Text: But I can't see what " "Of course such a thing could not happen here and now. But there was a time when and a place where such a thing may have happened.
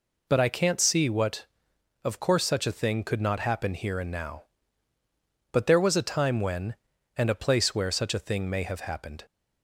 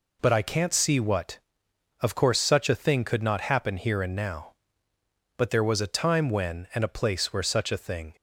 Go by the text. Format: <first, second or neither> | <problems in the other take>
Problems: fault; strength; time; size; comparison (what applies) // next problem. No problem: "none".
first | stops before "may have happened"; at 8.1 s